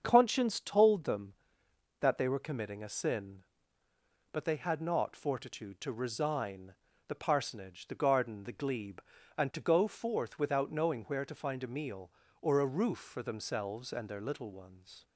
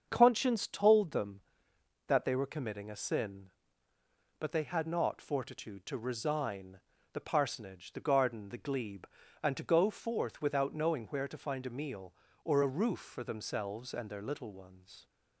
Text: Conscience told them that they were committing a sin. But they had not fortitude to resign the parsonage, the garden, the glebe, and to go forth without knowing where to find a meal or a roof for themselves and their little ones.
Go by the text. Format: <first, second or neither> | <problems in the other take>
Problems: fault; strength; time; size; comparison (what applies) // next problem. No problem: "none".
neither | starts louder than the rest; the same in both // pauses between "resign" and "the"; slight; the same in both